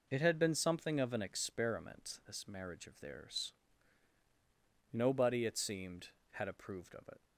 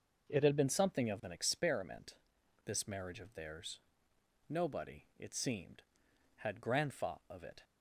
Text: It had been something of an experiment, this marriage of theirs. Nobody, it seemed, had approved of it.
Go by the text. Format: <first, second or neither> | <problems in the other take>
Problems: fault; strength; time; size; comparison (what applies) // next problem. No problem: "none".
first | says "grandfa" for "approved"; at 6.6 s